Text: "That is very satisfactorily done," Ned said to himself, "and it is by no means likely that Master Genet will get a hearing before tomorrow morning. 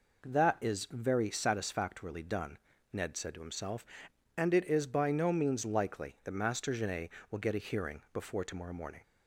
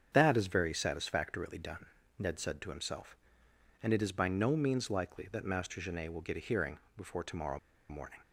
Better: first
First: none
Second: starts louder than the rest; strong; until 1.1 s; 7.5 dB // pauses between "hearing" and "before"; slight; at 6.7 s; 0.20 s long // pauses between "tomorrow" and "morning"; slight; at 7.5 s; 0.31 s long

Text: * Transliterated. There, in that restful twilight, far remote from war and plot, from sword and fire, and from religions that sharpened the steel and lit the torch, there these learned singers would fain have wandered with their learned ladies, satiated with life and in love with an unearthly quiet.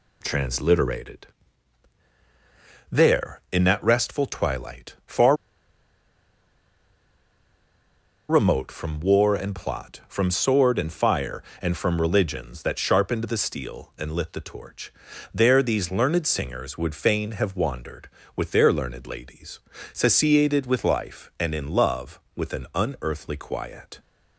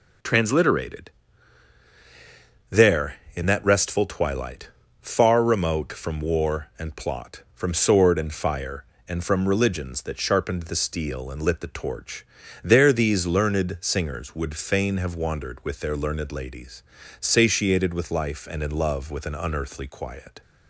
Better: second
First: pauses between "far" and "remote"; strong; at 5.3 s; 2.9 s long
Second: none

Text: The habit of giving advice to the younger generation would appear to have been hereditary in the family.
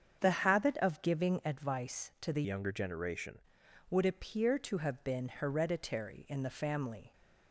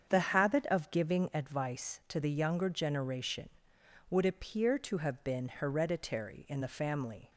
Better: second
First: starts louder than the rest; strong; until 1.2 s; 7.5 dB // changes voice from "younger" to "generation"; from 2.4 to 3.4 s; 1.0 s long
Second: starts louder than the rest; strong; until 1.1 s; 7.5 dB

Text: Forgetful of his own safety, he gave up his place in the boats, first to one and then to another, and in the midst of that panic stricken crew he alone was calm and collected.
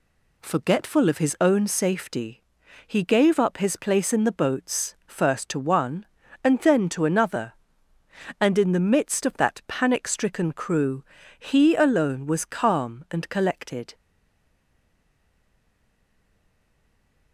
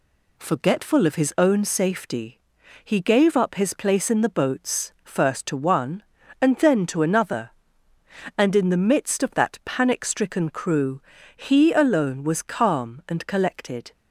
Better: second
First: pauses between "crew" and "he"; slight; at 11.0 s; 0.34 s long // stays silent after the last word; strong; from 13.9 s on; 3.4 s long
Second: pauses between "crew" and "he"; slight; at 11.0 s; 0.34 s long

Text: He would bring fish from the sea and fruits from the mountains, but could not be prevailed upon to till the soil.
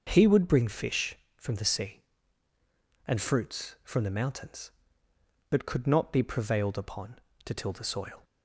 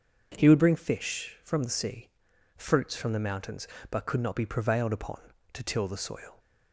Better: first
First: none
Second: skips "and"; at 2.3 s

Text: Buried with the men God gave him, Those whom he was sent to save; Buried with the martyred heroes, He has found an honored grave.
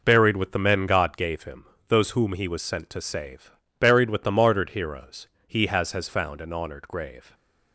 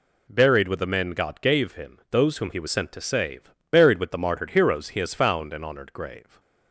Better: second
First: says "has" twice; at 5.9 s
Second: none

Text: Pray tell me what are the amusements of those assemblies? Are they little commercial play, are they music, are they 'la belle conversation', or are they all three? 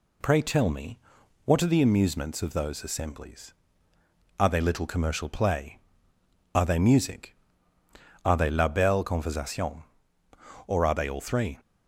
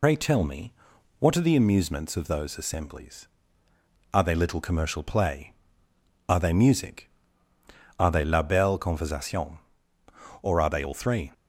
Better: first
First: pauses between "me" and "what"; noticeable; at 0.9 s; 0.46 s long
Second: loses the start of "Pray"; at 0.0 s; 80 ms // pauses between "me" and "what"; noticeable; at 0.7 s; 0.46 s long

